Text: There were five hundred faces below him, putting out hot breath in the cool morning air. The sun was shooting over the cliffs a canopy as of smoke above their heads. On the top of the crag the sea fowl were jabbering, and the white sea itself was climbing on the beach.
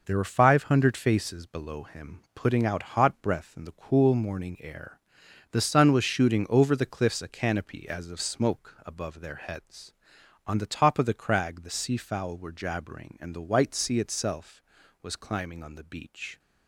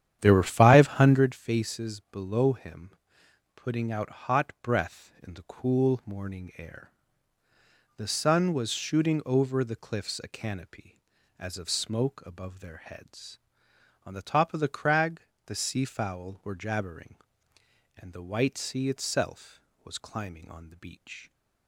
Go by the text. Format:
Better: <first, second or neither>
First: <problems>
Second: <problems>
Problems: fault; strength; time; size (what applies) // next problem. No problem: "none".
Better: first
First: none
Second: starts louder than the rest; strong; until 1.3 s; 10 dB // pauses between "crag" and "the"; slight; at 15.2 s; 0.24 s long